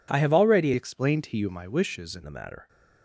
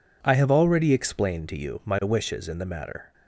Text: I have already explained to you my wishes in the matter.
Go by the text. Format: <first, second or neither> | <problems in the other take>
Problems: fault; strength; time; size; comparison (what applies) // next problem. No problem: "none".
second | changes voice from "explained" to "in"; from 0.7 to 2.2 s; 1.5 s long